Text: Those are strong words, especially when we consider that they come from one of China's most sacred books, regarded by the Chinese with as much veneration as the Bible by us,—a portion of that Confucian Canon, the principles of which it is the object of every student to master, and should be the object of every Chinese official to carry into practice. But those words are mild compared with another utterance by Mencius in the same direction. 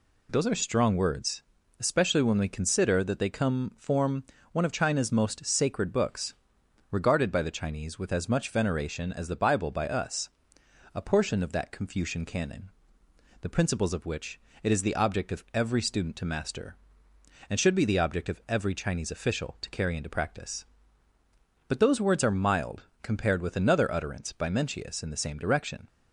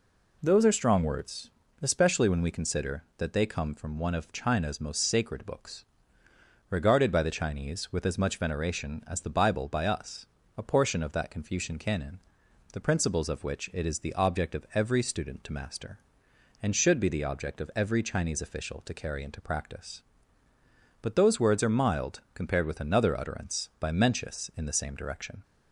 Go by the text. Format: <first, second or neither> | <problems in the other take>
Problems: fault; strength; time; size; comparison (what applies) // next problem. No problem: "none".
second | says "form" for "from"; at 3.7 s // pauses between "which" and "it"; slight; at 14.3 s; 0.24 s long // pauses between "mild" and "compared"; slight; at 22.8 s; 0.18 s long